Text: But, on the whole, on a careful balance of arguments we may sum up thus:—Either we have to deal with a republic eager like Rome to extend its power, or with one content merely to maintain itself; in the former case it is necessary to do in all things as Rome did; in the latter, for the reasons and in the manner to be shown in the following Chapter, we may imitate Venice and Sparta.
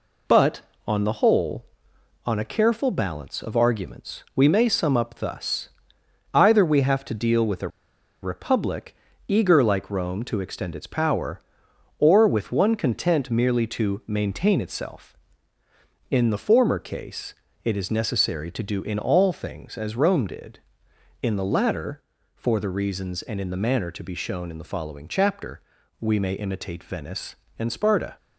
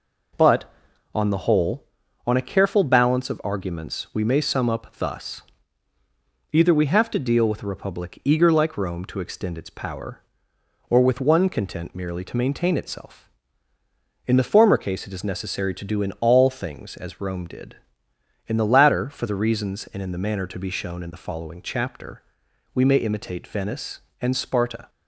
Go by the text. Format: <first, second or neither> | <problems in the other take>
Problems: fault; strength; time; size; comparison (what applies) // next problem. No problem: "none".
second | pauses between "a" and "republic"; noticeable; at 7.6 s; 0.54 s long // pauses between "republic" and "eager"; slight; at 8.9 s; 0.32 s long // pauses between "case" and "it"; slight; at 17.3 s; 0.28 s long